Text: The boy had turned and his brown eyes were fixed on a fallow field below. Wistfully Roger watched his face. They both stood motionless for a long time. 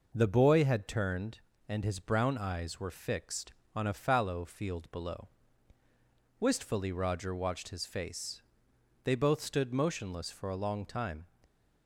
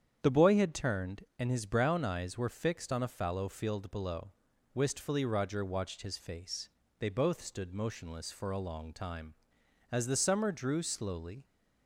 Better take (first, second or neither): first